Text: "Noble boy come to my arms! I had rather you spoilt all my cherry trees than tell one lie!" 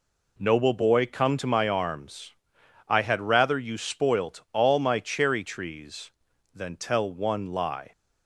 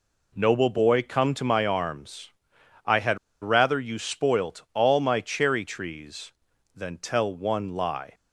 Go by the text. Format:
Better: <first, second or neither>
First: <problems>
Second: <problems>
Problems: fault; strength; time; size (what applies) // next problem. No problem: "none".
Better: first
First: none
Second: pauses between "had" and "rather"; slight; at 3.1 s; 0.23 s long